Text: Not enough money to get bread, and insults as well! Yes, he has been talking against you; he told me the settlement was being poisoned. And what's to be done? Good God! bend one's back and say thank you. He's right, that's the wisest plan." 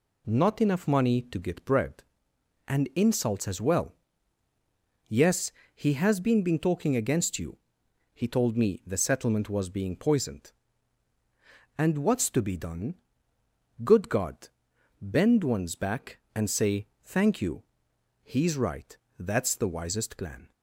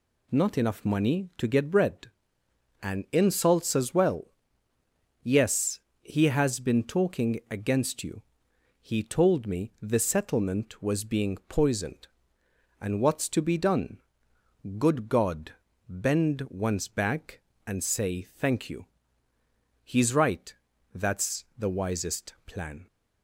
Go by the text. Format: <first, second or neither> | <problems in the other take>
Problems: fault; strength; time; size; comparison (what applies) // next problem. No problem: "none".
second | says "been" twice; at 6.4 s // pauses between "say" and "thank"; slight; at 16.8 s; 0.18 s long